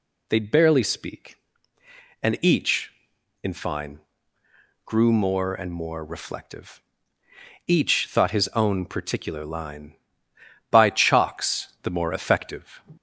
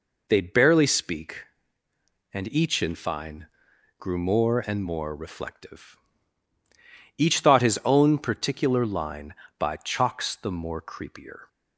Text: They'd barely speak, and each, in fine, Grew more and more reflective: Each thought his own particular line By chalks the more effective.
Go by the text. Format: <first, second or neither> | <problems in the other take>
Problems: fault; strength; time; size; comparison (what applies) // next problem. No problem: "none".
first | says "creepier" for "effective"; at 10.8 s